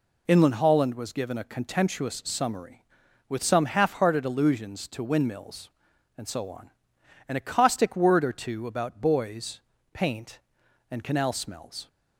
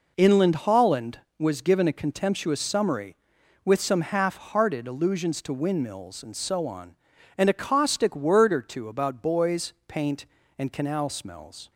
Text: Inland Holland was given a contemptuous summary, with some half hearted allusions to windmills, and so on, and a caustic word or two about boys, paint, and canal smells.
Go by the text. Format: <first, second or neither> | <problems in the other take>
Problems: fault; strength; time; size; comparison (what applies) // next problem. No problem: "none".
neither | none